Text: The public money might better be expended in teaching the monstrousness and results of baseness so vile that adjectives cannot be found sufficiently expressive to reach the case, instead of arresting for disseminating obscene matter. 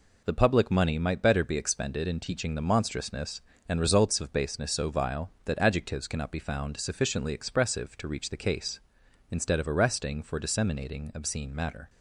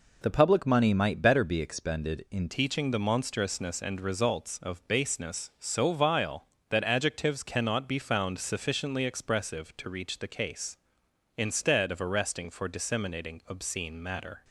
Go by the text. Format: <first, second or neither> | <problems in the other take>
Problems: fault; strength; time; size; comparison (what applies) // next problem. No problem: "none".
first | changes voice at "teaching"; from 2.4 s on; 12.0 s long